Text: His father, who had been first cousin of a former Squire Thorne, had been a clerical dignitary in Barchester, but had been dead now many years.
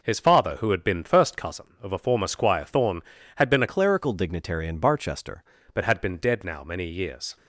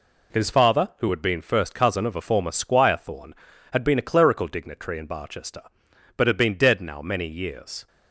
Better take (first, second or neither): second